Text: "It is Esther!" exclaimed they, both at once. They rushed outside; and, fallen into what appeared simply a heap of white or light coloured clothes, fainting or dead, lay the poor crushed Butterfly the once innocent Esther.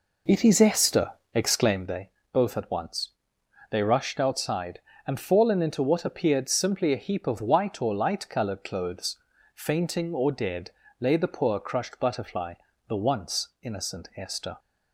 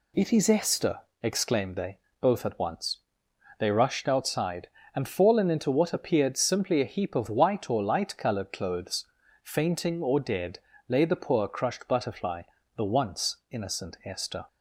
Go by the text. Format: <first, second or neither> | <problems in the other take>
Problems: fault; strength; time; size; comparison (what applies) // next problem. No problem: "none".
second | starts louder than the rest; noticeable; until 1.9 s; 4 dB // pauses between "Butterfly" and "the"; slight; at 12.5 s; 0.34 s long; slight in the second // pauses between "once" and "innocent"; slight; at 13.4 s; 0.16 s long; slight in the second